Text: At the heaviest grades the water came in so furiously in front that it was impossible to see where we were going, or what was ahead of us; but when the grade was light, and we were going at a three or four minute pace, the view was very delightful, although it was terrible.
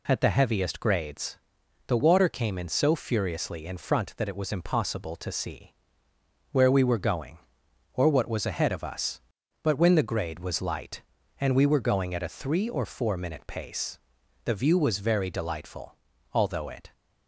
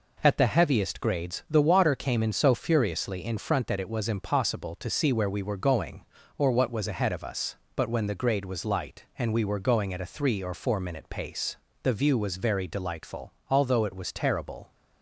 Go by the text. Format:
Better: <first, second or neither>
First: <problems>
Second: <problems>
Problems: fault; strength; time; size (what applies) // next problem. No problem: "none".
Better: second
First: pauses between "grades" and "the"; noticeable; at 1.3 s; 0.52 s long // pauses between "see" and "where"; noticeable; at 5.7 s; 0.78 s long // stops before "was terrible"; at 16.9 s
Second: none